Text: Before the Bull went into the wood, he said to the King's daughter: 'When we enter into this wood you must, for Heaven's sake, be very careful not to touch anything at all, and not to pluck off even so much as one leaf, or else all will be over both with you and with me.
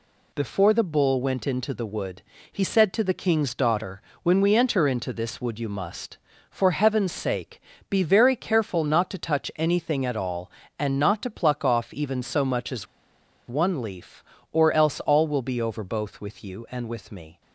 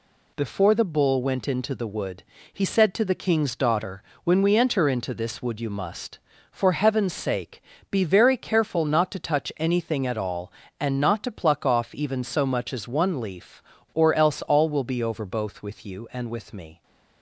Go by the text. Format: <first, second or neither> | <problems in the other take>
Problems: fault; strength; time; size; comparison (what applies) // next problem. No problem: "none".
second | pauses between "as" and "one"; noticeable; at 12.8 s; 0.62 s long